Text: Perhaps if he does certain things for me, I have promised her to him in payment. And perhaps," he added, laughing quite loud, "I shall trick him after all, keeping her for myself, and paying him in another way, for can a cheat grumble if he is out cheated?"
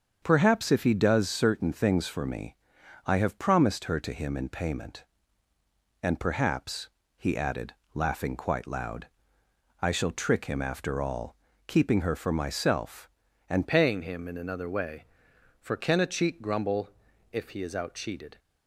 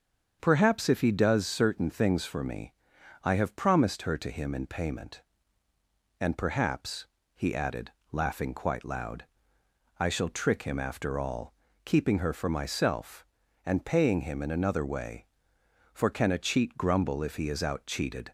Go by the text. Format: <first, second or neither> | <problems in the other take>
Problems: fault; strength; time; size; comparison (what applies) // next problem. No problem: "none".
second | starts louder than the rest; strong; until 1.2 s; 7 dB; strong in the second // changes voice at "paying"; from 13.6 s on; 4.7 s long // pauses between "grumble" and "if"; at 16.8 s; 0.42 s long